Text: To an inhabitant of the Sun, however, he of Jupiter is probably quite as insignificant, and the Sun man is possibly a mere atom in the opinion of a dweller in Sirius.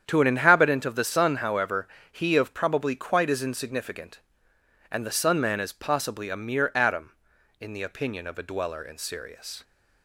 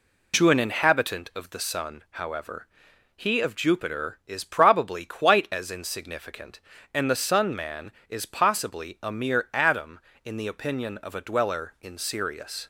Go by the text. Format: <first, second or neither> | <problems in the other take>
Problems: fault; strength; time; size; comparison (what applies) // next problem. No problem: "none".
second | starts louder than the rest; strong; until 1.0 s; 8.5 dB // skips "Jupiter is"; at 2.5 s